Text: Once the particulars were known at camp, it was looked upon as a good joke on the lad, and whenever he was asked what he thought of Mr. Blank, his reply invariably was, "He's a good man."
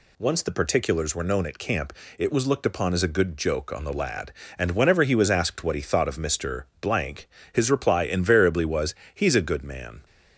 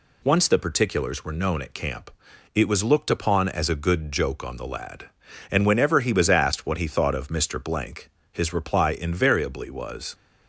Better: first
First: none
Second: stops before "He's a good man"; at 10.1 s

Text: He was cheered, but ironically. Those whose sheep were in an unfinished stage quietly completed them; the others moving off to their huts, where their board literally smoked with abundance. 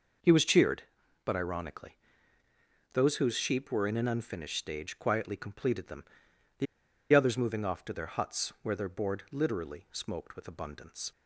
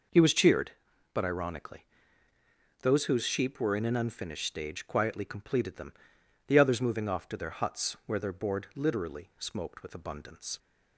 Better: second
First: starts louder than the rest; noticeable; until 1.6 s; 6 dB // pauses between "the" and "others"; noticeable; at 6.6 s; 0.47 s long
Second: none

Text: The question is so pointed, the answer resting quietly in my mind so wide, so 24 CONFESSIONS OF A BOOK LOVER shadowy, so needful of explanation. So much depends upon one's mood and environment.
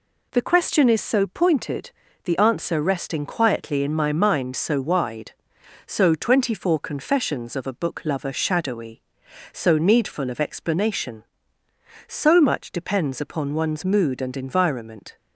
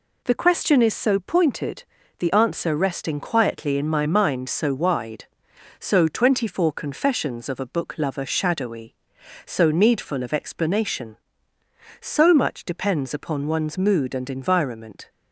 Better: neither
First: none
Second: none

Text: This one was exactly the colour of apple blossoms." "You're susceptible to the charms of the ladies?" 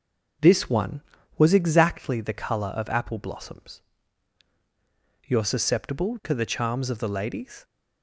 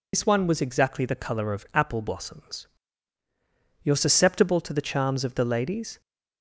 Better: first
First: none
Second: loses the start of "This"; at 0.1 s; 80 ms

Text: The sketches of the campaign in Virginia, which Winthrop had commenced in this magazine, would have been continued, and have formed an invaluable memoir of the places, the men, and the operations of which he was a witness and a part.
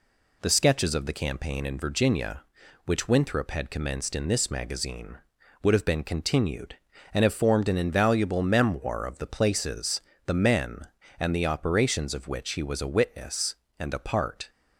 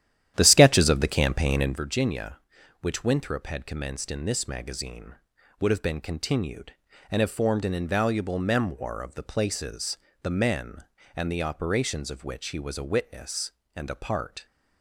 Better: first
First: none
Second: starts louder than the rest; strong; until 1.8 s; 11 dB

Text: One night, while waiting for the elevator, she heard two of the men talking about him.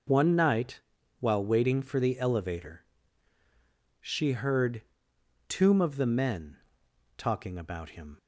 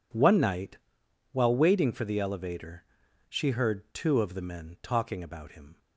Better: second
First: says "tomb" for "two"; at 5.4 s // pauses between "men" and "talking"; noticeable; at 6.5 s; 0.58 s long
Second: none

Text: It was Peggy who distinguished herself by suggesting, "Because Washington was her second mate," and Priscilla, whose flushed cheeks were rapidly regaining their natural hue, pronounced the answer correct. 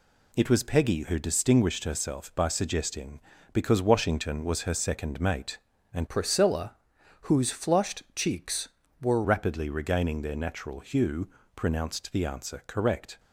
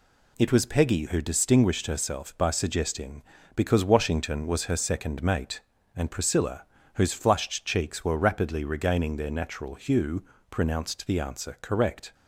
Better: second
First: changes voice from "Priscilla" to "were"; from 6.0 to 9.2 s; 3.2 s long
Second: none

